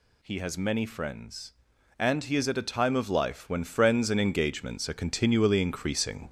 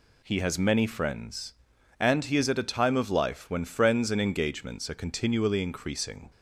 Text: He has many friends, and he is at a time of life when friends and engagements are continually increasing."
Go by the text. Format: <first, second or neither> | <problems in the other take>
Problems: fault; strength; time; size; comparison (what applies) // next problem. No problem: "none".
second | gets louder; throughout; 3.5 dB